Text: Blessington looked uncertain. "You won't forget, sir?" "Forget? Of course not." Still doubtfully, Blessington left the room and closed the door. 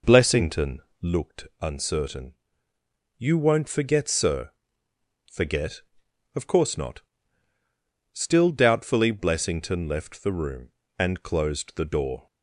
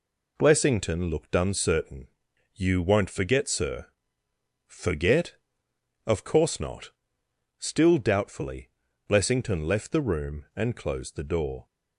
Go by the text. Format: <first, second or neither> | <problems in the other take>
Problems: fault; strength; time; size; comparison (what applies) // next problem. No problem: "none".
second | starts louder than the rest; noticeable; until 1.2 s; 4.5 dB // pauses between "Blessington" and "looked"; slight; at 0.8 s; 0.18 s long // pauses between "looked" and "uncertain"; slight; at 1.4 s; 0.16 s long